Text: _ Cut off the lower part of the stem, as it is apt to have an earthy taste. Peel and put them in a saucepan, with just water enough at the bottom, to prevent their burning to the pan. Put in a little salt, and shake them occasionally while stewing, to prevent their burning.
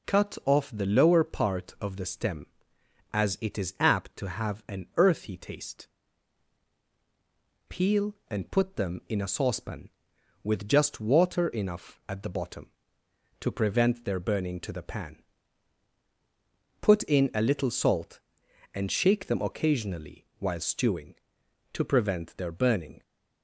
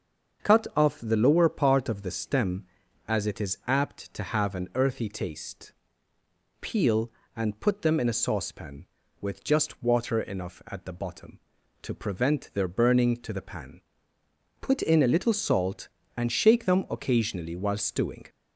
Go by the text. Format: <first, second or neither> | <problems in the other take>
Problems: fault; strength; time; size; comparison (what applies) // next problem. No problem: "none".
first | starts louder than the rest; until 1.5 s; 7 dB // stops before "to prevent their burning"; at 18.2 s